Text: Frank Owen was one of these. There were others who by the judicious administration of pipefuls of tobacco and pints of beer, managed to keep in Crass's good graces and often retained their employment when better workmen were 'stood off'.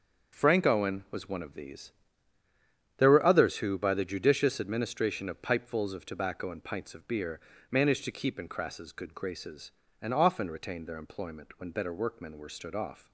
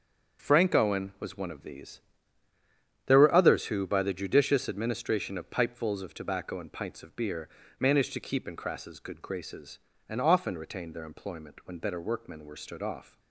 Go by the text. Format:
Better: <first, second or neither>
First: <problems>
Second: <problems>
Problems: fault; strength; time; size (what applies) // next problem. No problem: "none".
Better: neither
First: starts louder than the rest; until 1.4 s; 6.5 dB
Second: starts louder than the rest; until 1.4 s; 6.5 dB